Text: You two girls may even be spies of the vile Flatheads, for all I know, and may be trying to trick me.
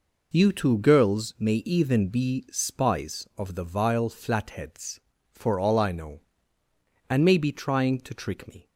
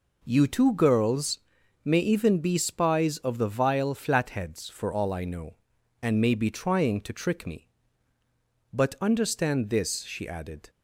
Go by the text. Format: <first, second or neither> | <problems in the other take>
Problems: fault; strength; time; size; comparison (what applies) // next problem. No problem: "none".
first | pauses between "girls" and "may"; at 1.3 s; 0.44 s long // goes on to say "But understand this she added"; strong; from 8.7 s on; 1.9 s long